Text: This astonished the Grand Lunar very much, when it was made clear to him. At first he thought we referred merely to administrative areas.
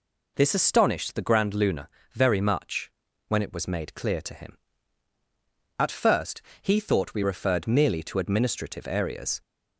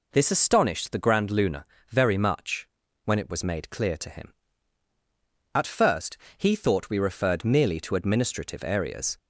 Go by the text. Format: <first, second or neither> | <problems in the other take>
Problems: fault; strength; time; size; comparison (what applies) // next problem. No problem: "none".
neither | pauses between "Lunar" and "very"; slight; the same in both // pauses between "first" and "he"; slight; the same in both